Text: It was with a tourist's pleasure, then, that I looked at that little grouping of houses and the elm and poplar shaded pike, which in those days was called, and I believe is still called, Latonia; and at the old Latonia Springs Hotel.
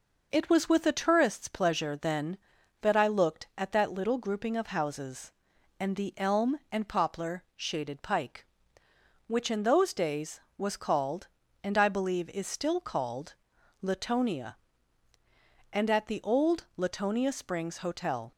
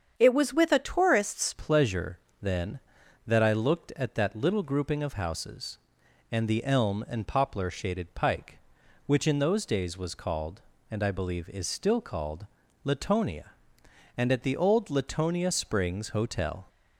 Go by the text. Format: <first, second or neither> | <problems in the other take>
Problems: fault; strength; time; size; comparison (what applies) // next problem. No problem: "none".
first | starts louder than the rest; strong; until 1.1 s; 7.5 dB // changes voice at "pleasure"; from 1.5 s on; 15.1 s long